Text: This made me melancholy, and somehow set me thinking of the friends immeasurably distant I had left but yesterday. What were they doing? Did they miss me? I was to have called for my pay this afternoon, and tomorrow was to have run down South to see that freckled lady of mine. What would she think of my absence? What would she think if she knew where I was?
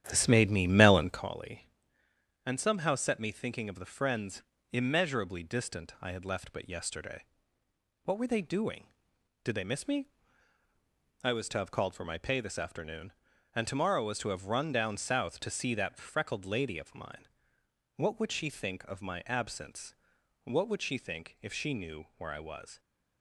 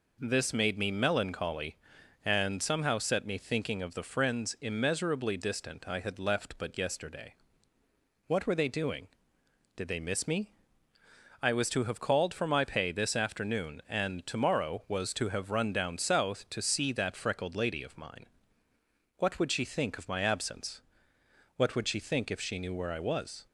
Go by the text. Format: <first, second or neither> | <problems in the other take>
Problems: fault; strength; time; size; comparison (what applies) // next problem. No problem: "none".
second | starts louder than the rest; strong; until 1.3 s; 10.5 dB // pauses between "friends" and "immeasurably"; slight; at 4.4 s; 0.28 s long